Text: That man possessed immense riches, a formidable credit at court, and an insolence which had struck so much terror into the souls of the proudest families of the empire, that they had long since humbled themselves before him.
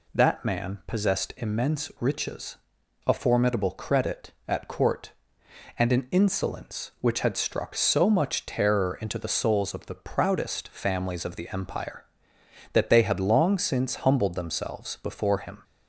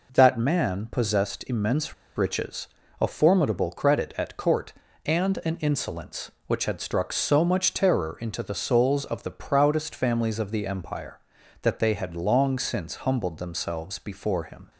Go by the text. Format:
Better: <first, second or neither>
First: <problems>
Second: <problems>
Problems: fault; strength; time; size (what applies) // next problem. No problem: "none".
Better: first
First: none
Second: pauses between "immense" and "riches"; slight; at 1.9 s; 0.22 s long